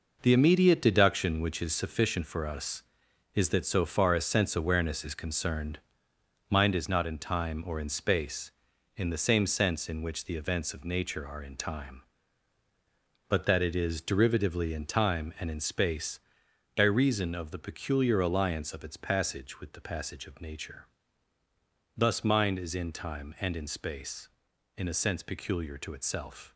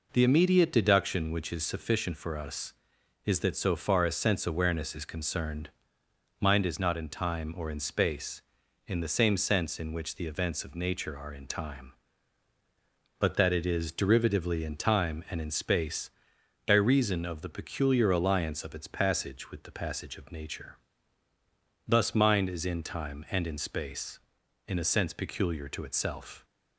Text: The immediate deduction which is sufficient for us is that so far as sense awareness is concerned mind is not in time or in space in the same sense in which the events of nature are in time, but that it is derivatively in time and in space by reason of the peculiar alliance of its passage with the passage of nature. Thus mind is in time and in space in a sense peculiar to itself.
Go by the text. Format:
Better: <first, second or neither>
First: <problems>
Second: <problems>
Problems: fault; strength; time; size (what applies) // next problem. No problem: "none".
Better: second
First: gets quieter; strong; throughout; 8 dB // pauses between "concerned" and "mind"; noticeable; at 5.7 s; 0.72 s long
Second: pauses between "concerned" and "mind"; noticeable; at 5.6 s; 0.72 s long